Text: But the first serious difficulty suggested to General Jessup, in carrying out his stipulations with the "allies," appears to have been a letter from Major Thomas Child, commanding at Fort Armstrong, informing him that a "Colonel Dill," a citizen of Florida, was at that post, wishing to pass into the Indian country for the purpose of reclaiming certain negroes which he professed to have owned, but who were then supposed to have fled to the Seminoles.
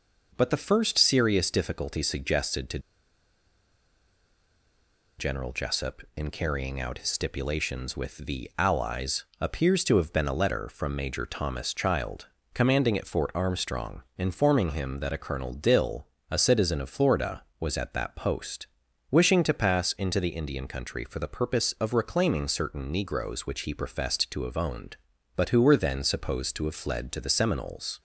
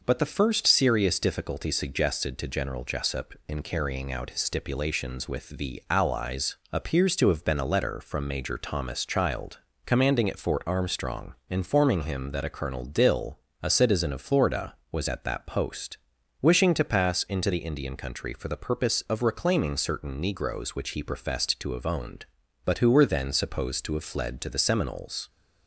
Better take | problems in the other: second | pauses between "to" and "General"; strong; at 2.7 s; 2.3 s long

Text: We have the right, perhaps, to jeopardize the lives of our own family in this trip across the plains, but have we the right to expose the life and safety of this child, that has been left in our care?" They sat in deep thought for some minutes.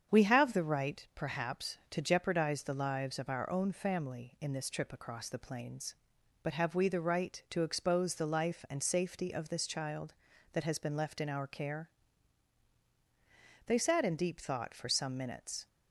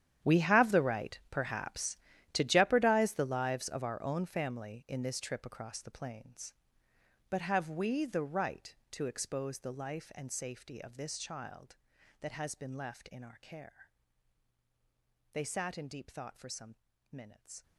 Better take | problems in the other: first | gets quieter; strong; throughout; 17 dB // starts louder than the rest; strong; until 1.3 s; 10 dB; strong in the first // pauses between "some" and "minutes"; slight; at 16.7 s; 0.36 s long

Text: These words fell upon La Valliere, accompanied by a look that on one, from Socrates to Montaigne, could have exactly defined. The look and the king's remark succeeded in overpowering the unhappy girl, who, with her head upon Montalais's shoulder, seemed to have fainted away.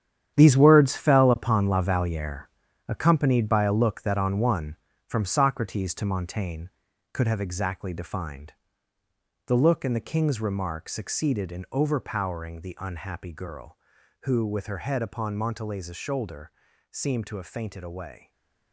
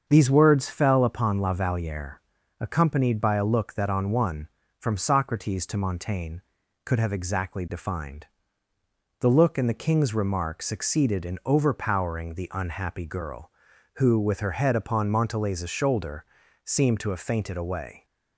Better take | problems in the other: second | gets quieter; strong; throughout; 11 dB // starts louder than the rest; strong; until 1.4 s; 9.5 dB; also in the second // stays silent after the last word; slight; from 18.1 s on; 0.6 s long

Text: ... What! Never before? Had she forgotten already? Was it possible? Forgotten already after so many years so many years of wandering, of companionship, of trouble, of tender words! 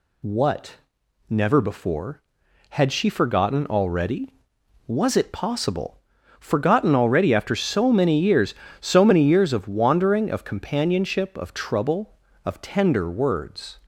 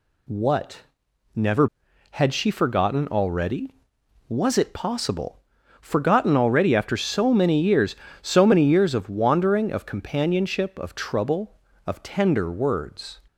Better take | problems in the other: first | skips "before"; at 1.8 s

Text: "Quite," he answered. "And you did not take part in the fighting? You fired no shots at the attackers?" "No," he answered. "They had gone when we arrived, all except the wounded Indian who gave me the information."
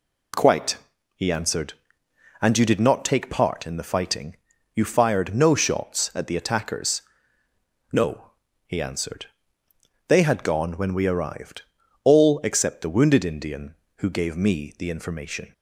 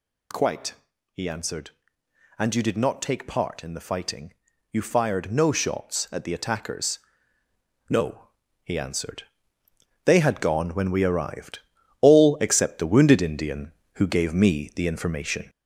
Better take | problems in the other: first | gets louder; noticeable; throughout; 5 dB

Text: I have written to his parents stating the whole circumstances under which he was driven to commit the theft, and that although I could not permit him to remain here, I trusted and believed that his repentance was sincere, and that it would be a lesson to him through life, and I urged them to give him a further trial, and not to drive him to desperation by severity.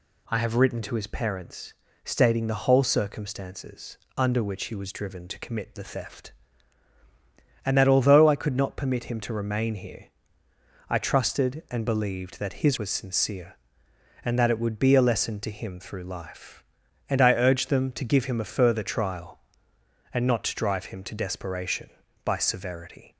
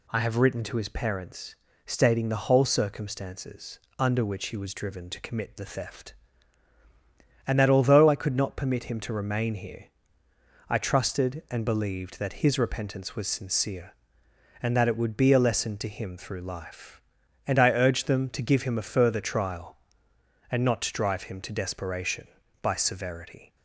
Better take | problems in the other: second | pauses between "parents" and "stating"; slight; at 1.7 s; 0.30 s long; slight in the second // pauses between "circumstances" and "under"; slight; at 3.9 s; 0.22 s long; slight in the second // skips "repentance"; at 12.7 s

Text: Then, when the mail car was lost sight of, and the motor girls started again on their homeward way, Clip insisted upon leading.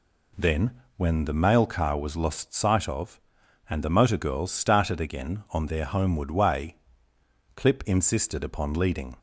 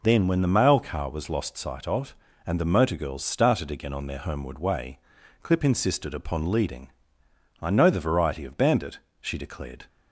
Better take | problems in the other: first | goes on to say "I know the variety of bandit she declared"; strong; from 7.6 s on; 2.2 s long

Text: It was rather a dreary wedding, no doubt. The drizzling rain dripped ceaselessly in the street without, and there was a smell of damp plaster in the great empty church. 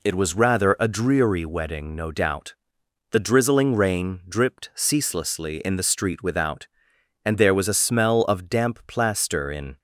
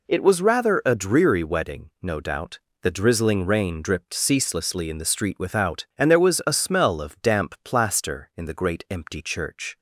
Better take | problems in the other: second | stops before "the great empty church"; at 9.7 s

